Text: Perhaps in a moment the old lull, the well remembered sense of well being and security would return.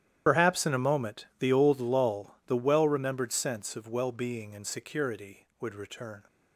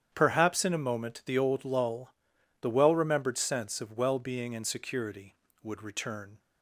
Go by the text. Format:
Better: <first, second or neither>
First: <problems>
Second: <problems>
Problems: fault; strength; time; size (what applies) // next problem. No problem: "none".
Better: second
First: loses the start of "Perhaps"; at 0.2 s; 55 ms // starts louder than the rest; strong; until 1.2 s; 11 dB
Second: starts louder than the rest; strong; until 1.1 s; 9 dB